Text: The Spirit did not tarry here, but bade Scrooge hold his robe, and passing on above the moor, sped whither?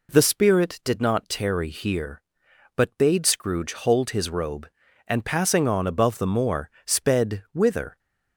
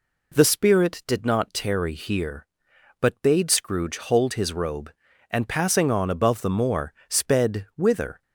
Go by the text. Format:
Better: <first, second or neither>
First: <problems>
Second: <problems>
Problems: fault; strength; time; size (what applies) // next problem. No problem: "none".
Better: neither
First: none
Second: none